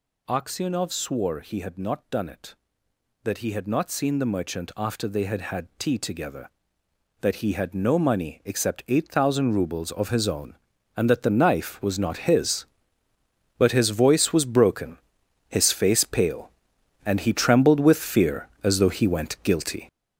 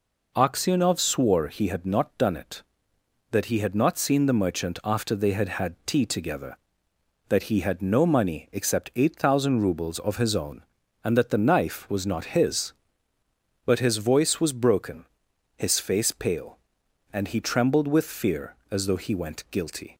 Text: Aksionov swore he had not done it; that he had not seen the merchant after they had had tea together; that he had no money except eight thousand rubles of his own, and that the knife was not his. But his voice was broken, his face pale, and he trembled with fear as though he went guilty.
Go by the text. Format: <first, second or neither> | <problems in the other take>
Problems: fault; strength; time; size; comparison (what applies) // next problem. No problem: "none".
second | gets louder; strong; throughout; 8 dB